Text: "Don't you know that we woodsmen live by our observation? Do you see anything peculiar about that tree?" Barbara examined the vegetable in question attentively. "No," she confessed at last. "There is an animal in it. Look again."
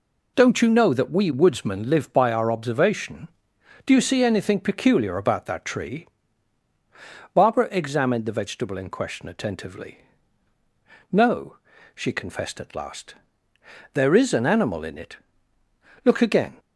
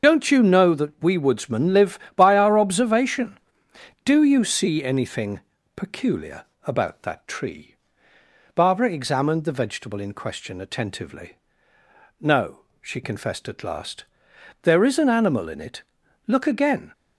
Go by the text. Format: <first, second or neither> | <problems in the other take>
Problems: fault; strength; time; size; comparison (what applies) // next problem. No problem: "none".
first | loses the start of "Don't"; at 0.0 s; 50 ms // starts louder than the rest; until 1.1 s; 6.5 dB // pauses between "anything" and "peculiar"; slight; at 5.4 s; 0.34 s long // pauses between "peculiar" and "about"; slight; at 6.4 s; 0.19 s long